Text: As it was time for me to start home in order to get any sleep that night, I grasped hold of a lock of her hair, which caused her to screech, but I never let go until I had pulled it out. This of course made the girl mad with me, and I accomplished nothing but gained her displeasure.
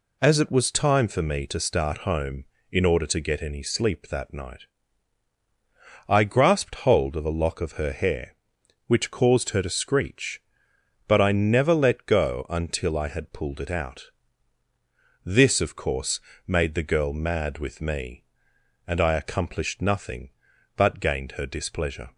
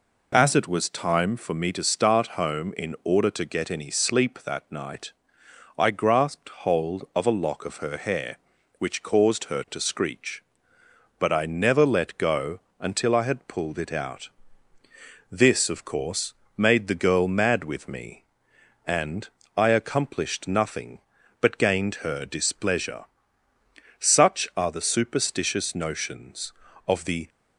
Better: first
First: pauses between "course" and "made"; slight; at 16.1 s; 0.28 s long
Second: pauses between "go" and "until"; slight; at 12.5 s; 0.20 s long // pauses between "course" and "made"; slight; at 16.3 s; 0.20 s long // pauses between "and" and "I"; slight; at 19.2 s; 0.30 s long // goes on to say "Such are the superstitious notions of the"; strong; from 23.9 s on; 3.3 s long

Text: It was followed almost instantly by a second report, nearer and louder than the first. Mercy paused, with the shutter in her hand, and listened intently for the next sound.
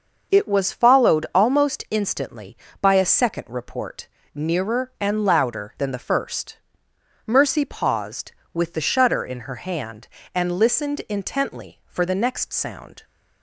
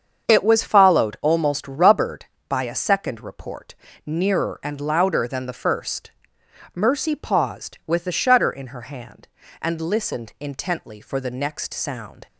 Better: first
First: starts louder than the rest; until 1.4 s; 6 dB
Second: starts louder than the rest; strong; until 1.3 s; 7 dB // says "rubbered" for "instantly"; at 1.6 s

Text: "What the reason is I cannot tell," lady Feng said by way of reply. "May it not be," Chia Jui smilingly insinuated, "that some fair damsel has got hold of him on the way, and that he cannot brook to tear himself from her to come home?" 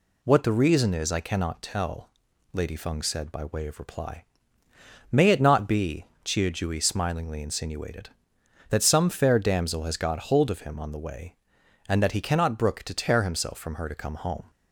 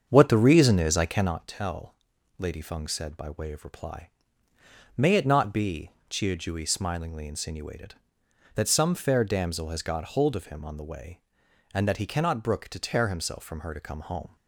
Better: first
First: none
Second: starts louder than the rest; strong; until 1.4 s; 7 dB

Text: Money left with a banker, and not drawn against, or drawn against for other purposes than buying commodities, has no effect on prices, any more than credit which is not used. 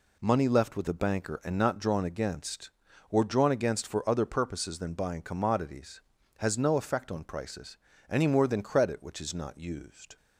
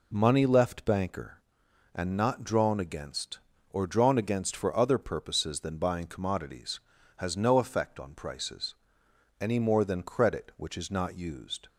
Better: first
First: none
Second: skips "with a"; at 0.8 s

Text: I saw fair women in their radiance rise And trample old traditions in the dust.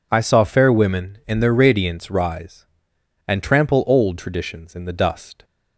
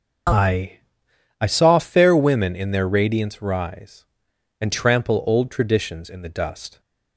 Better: first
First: none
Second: says "I" twice; at 1.3 s

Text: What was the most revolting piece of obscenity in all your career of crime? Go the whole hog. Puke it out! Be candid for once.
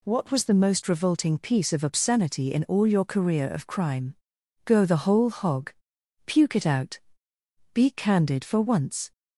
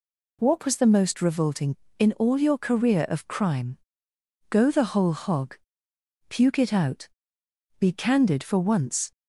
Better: first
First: none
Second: skips "piece of obscenity"; at 1.8 s

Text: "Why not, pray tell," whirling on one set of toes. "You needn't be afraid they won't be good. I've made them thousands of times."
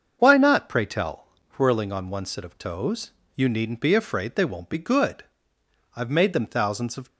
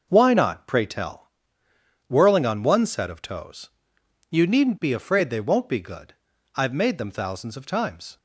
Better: second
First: starts louder than the rest; until 1.1 s; 6.5 dB // stops before "times"; at 7.0 s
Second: none

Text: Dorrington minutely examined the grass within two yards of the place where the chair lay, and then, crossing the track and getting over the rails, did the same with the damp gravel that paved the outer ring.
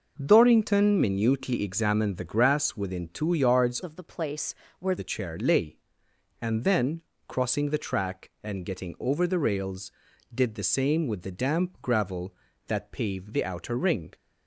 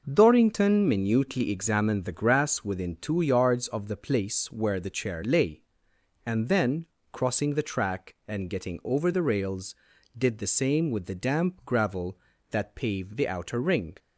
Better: second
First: changes voice from "of" to "where"; from 3.8 to 4.9 s; 1.1 s long // pauses between "place" and "where"; slight; at 4.5 s; 0.26 s long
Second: none

